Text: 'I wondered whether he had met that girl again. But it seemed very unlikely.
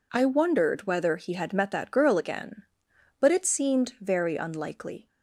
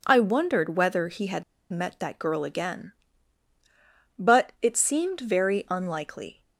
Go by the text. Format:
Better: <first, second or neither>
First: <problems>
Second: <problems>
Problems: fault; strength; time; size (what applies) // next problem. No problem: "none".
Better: first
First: none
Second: pauses between "had" and "met"; slight; at 1.4 s; 0.28 s long